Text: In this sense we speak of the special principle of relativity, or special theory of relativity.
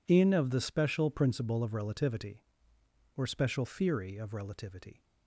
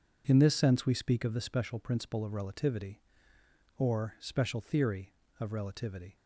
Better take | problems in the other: second | skips "this sense we speak"; at 0.3 s

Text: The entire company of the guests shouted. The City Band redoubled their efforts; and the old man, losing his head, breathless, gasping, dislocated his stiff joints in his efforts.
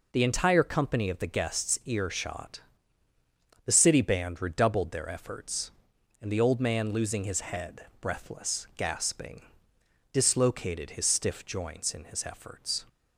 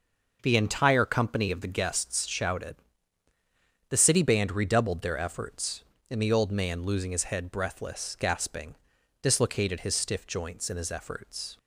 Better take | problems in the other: second | says "earshot" for "shouted"; at 1.8 s

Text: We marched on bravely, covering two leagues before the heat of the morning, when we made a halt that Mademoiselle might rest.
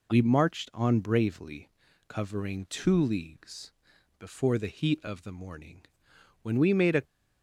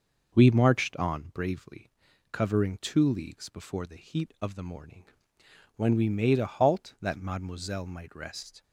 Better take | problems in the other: second | pauses between "leagues" and "before"; noticeable; at 3.7 s; 0.46 s long // stops before "halt that Mademoiselle might rest"; at 7.0 s

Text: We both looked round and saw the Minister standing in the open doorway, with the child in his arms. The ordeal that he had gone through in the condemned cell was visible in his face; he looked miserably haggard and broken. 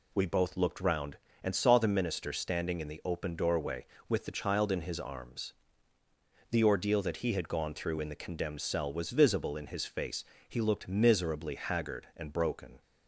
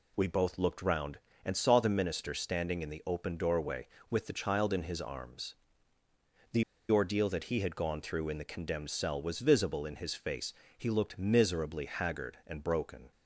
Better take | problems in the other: first | pauses between "The" and "ordeal"; slight; at 6.6 s; 0.27 s long

